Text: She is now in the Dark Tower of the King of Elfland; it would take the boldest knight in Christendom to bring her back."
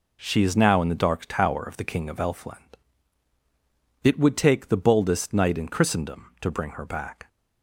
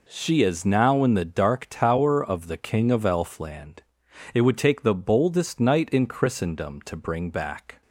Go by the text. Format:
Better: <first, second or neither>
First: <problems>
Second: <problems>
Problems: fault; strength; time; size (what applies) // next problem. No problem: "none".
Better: first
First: none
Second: skips "her"; at 7.2 s